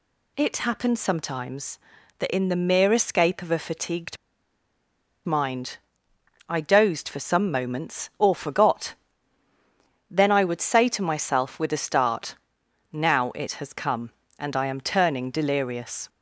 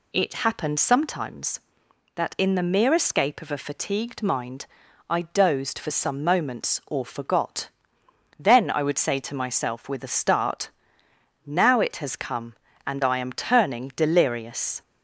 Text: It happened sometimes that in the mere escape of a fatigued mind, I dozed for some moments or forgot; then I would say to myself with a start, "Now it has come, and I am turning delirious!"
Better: second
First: pauses between "fatigued" and "mind"; at 4.1 s; 1.0 s long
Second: none

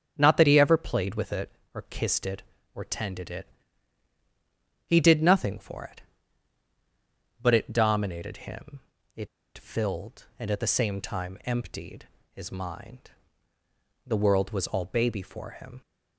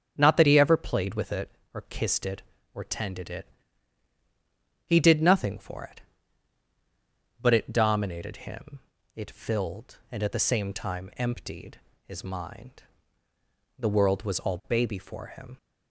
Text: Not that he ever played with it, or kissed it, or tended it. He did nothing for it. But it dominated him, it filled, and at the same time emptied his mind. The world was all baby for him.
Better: second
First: starts louder than the rest; strong; until 1.1 s; 8 dB // pauses between "it" and "filled"; slight; at 9.2 s; 0.28 s long // pauses between "emptied" and "his"; slight; at 12.0 s; 0.26 s long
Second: starts louder than the rest; strong; until 1.1 s; 8 dB // pauses between "emptied" and "his"; slight; at 11.7 s; 0.26 s long

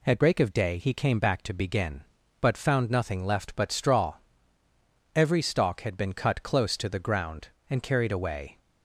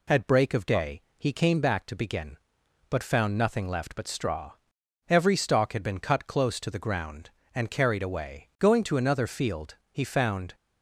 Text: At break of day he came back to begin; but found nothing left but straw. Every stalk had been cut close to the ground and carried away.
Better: first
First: none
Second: pauses between "day" and "he"; slight; at 1.0 s; 0.16 s long // goes on to say "Going to another field he found"; strong; from 8.5 s on; 1.9 s long

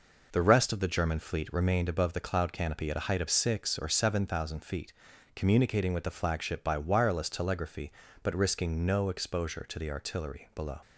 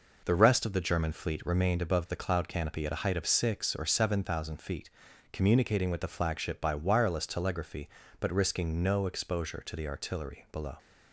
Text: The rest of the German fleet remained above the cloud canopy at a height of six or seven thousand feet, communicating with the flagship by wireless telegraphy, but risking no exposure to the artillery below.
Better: neither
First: none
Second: none

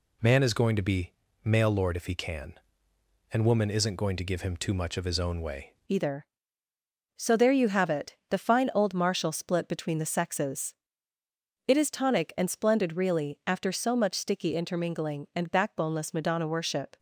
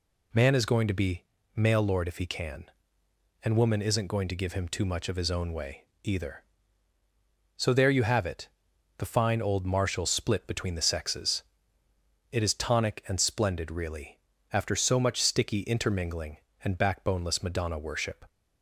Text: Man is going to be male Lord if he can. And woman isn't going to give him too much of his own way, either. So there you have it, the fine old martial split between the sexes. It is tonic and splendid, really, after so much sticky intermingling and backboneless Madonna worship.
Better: second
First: pauses between "be" and "male"; slight; at 1.1 s; 0.34 s long // changes voice at "either"; from 5.8 s on; 11.1 s long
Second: pauses between "be" and "male"; slight; at 1.2 s; 0.34 s long

